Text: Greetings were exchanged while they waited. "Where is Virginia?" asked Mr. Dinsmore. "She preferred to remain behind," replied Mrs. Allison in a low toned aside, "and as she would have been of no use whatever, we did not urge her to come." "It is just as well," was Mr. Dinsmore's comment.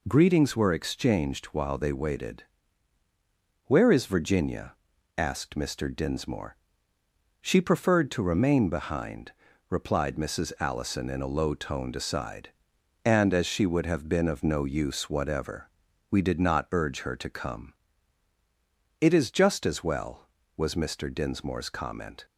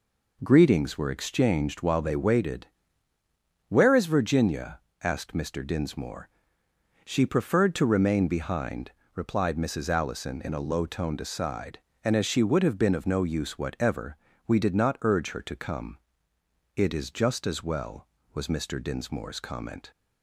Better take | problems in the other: neither | none

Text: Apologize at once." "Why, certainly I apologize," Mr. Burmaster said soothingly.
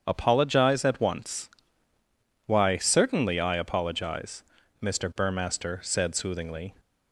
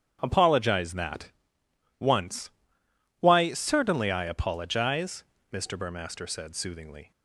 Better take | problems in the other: first | starts louder than the rest; strong; until 1.2 s; 8.5 dB; strong in the first // says "that" for "at"; at 0.9 s

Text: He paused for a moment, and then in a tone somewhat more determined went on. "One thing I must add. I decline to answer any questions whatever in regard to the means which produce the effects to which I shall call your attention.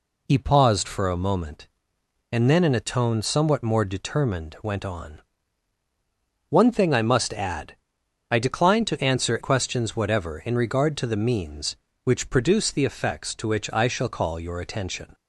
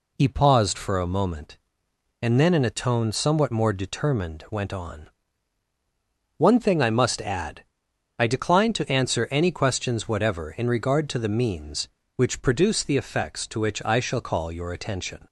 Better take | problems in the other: second | skips "any"; at 9.3 s

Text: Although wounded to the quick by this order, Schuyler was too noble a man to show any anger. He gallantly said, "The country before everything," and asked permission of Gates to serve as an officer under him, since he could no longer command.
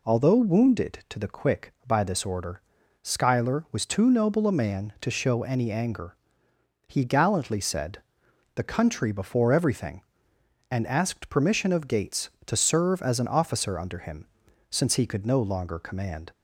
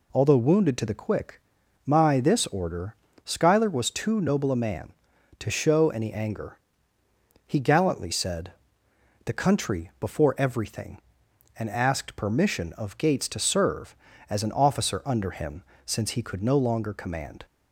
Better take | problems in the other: first | says "my" for "by"; at 1.8 s

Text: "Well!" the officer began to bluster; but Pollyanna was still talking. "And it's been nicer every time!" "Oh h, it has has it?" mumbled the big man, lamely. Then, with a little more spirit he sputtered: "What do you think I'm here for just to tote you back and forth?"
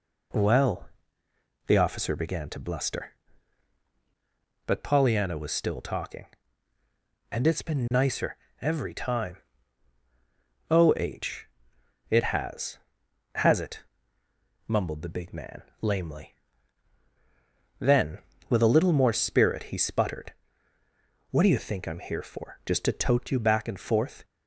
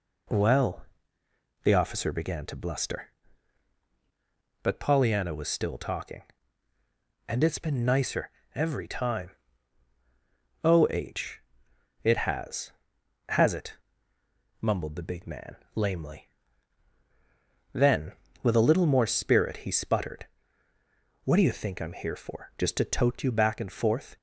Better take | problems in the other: neither | pauses between "nicer" and "every"; slight; the same in both

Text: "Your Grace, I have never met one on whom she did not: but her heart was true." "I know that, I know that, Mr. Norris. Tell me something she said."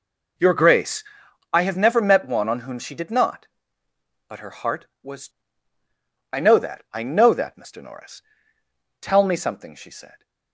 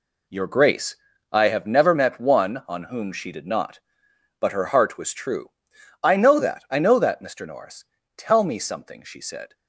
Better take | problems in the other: second | skips "true"; at 5.8 s

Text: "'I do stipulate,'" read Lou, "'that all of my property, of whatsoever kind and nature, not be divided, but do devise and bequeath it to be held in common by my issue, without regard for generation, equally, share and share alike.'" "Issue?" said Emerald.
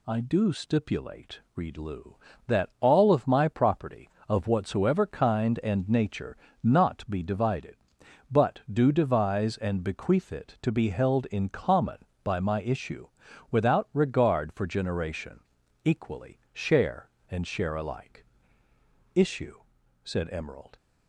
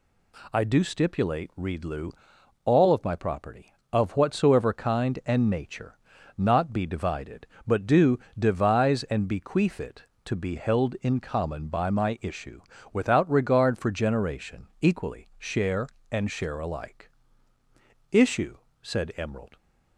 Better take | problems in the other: first | skips "that"; at 2.3 s // pauses between "do" and "devise"; slight; at 8.1 s; 0.20 s long

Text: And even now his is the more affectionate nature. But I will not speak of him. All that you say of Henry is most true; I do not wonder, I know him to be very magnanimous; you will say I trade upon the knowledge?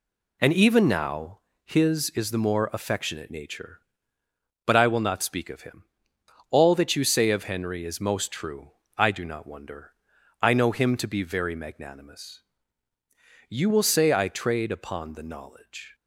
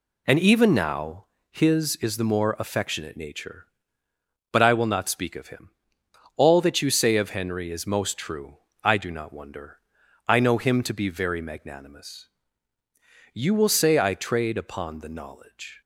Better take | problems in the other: neither | pauses between "now" and "his"; slight; the same in both

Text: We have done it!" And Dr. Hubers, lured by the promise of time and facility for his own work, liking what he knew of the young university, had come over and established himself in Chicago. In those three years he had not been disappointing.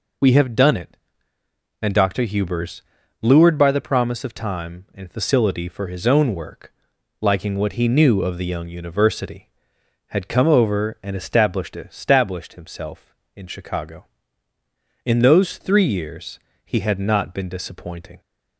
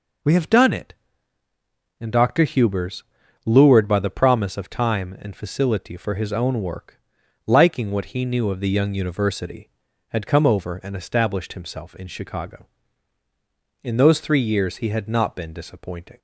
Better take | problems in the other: second | says "established" twice; at 11.7 s // pauses between "years" and "he"; slight; at 16.3 s; 0.26 s long

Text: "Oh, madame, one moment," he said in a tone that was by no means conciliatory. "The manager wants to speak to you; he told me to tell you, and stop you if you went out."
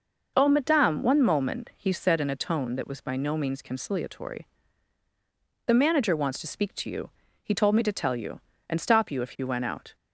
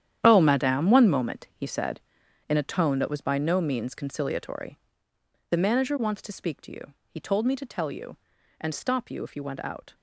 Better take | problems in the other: first | gets quieter; strong; throughout; 13.5 dB

